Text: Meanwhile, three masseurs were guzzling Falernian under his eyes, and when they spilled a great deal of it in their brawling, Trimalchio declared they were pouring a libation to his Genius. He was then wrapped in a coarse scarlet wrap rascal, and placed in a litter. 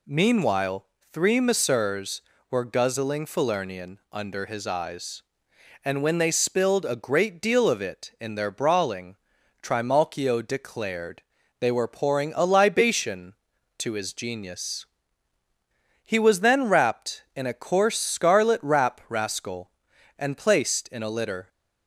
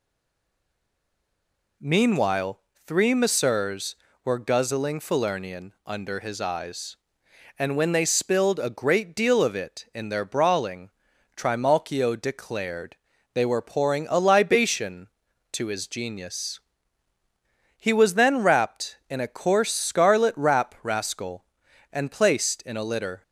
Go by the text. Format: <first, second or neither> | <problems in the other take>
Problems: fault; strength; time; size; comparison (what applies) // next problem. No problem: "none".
first | stays silent before the first word; noticeable; until 1.8 s; 1.8 s long // pauses between "declared" and "they"; at 12.9 s; 0.38 s long; also in the first